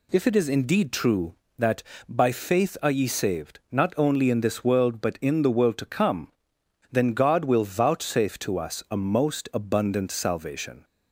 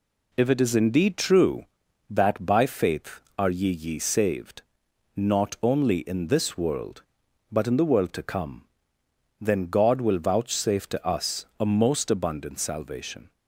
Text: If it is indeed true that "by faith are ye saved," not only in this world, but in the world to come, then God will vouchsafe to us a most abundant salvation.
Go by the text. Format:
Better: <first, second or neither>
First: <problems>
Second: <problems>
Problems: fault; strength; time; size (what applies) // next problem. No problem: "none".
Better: first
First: none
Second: says "ye" twice; at 3.6 s // pauses between "us" and "a"; slight; at 11.4 s; 0.16 s long